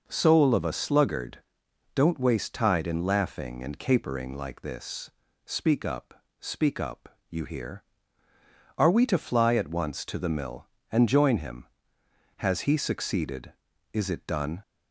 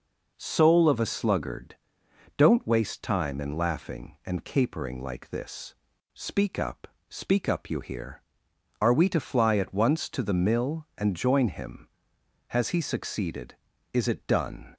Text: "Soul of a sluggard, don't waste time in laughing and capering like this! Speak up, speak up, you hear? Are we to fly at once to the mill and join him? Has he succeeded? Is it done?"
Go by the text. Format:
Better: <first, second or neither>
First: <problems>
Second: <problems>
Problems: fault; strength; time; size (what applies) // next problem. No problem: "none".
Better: second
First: says "tide" for "time"; at 2.5 s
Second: none